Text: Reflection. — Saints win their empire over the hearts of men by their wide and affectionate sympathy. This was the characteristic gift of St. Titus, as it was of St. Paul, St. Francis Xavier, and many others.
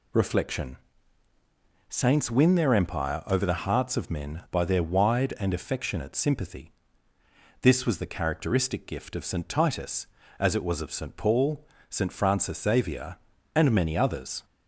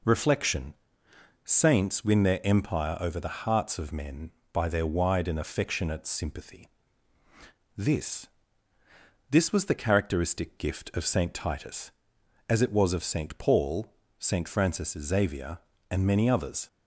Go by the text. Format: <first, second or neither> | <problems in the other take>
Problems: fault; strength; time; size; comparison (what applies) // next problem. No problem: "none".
first | says "This" twice; at 9.3 s